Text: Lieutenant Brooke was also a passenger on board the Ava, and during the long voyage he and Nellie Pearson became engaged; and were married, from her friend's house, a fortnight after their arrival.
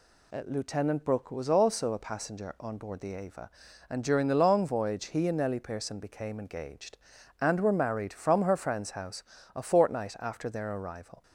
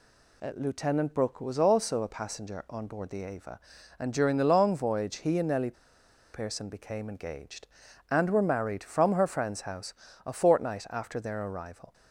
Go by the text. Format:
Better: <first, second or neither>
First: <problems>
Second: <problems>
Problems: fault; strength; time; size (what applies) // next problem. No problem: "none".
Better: first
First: none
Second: pauses between "Nellie" and "Pearson"; noticeable; at 5.7 s; 0.61 s long